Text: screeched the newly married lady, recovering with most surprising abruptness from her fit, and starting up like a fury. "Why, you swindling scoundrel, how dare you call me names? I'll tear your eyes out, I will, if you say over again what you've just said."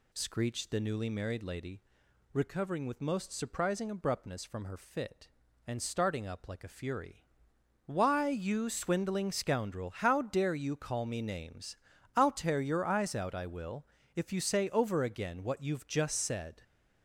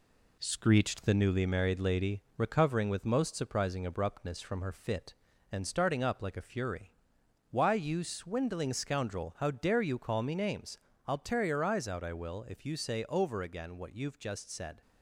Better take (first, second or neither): first